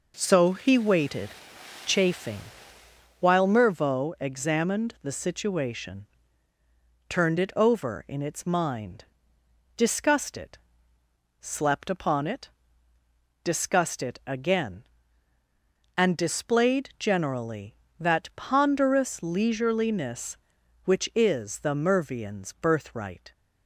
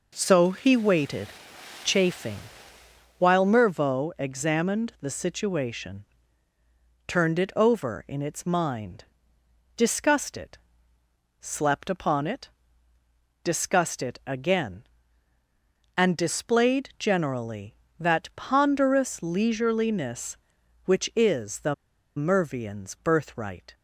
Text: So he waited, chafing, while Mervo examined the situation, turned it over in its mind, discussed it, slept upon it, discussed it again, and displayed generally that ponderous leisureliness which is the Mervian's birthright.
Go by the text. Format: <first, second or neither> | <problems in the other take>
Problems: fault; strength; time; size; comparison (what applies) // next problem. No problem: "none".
first | pauses between "the" and "Mervian's"; at 21.7 s; 0.42 s long